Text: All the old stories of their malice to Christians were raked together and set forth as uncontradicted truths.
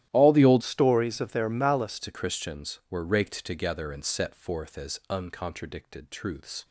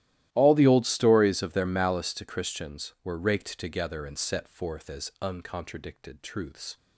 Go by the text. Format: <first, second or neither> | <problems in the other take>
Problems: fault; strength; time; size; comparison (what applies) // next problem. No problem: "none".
second | starts louder than the rest; strong; until 1.1 s; 13 dB; strong in the second // changes voice from "stories" to "malice"; from 0.6 to 1.9 s; 1.3 s long